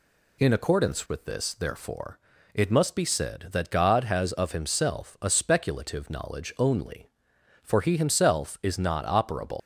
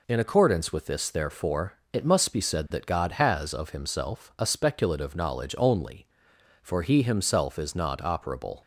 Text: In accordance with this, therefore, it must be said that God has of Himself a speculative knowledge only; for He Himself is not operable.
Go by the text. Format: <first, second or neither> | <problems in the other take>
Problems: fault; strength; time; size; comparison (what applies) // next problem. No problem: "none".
second | leaves "operable" unfinished; at 9.5 s; 100 ms